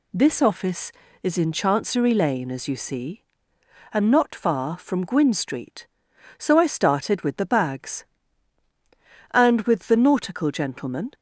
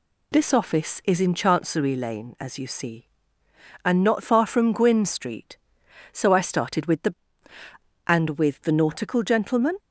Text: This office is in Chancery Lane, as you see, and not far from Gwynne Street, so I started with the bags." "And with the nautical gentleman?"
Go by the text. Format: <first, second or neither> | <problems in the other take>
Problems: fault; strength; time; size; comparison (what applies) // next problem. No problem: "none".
first | skips "bags"; at 7.5 s